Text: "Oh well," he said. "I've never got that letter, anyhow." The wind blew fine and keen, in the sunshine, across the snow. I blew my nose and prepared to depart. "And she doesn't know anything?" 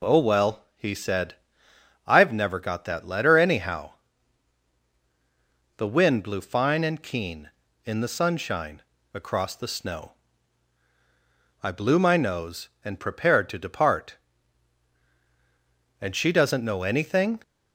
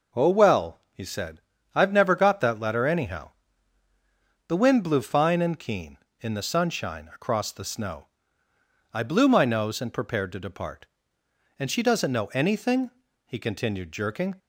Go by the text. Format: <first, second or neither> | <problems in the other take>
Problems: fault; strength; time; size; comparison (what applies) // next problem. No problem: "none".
first | goes on to say "he continued jerking"; noticeable; from 13.2 s on; 1.1 s long